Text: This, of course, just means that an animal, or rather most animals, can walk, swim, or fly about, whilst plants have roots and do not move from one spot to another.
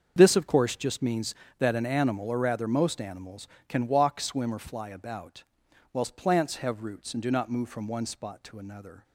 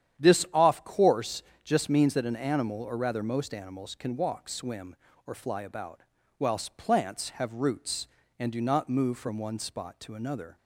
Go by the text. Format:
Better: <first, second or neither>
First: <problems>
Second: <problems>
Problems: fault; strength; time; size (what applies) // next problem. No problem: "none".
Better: first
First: starts louder than the rest; until 1.1 s; 7 dB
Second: starts louder than the rest; strong; until 1.2 s; 10 dB // says "off" for "of"; at 0.5 s